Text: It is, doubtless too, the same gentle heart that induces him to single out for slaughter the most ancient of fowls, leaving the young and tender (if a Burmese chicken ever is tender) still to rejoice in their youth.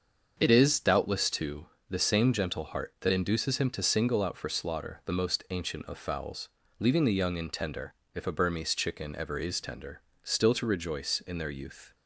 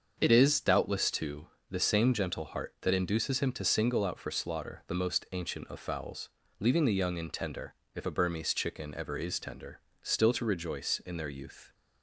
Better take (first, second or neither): neither